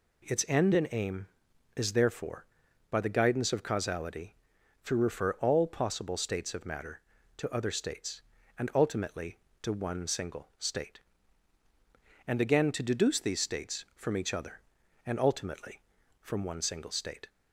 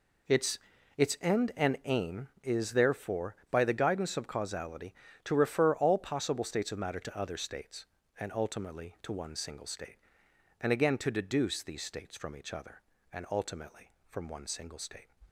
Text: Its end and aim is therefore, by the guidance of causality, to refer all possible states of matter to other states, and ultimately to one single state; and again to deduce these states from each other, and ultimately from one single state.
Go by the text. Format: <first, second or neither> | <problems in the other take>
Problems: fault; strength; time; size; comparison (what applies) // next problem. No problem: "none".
first | says "Its" twice; at 0.9 s